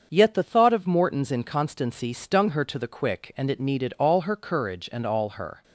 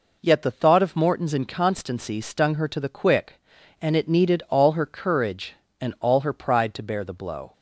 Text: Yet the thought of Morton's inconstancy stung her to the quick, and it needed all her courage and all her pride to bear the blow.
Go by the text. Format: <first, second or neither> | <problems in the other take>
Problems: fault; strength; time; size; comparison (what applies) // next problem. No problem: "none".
second | starts louder than the rest; until 1.1 s; 7 dB // stops before "pride to bear the blow"; at 5.6 s